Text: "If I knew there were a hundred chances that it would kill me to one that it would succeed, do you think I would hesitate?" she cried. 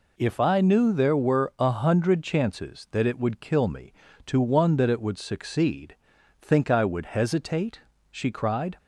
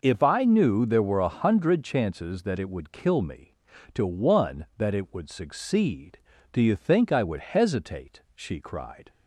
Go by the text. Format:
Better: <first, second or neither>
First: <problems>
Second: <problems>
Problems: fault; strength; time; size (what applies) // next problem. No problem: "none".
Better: second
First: skips "do you"; at 6.1 s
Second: none